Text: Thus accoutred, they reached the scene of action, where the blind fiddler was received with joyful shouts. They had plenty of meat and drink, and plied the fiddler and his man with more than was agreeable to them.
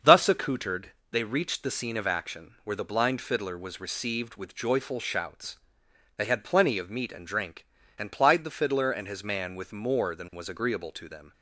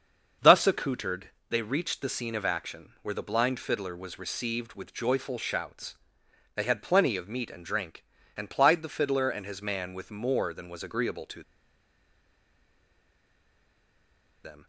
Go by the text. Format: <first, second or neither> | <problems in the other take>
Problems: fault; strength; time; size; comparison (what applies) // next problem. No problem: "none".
first | starts louder than the rest; until 1.5 s; 6.5 dB; also in the first // pauses between "to" and "them"; strong; at 11.4 s; 3.0 s long